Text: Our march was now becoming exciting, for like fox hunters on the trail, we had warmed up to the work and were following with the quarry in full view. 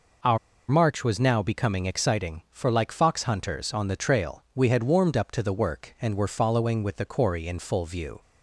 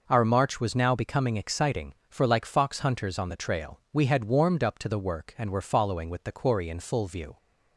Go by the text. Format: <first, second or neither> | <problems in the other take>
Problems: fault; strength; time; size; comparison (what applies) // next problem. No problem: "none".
second | pauses between "Our" and "march"; slight; at 0.3 s; 0.32 s long